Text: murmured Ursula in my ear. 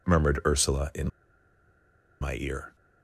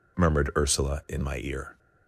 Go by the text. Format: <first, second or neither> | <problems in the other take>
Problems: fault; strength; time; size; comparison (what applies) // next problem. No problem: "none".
second | pauses between "in" and "my"; at 1.0 s; 1.1 s long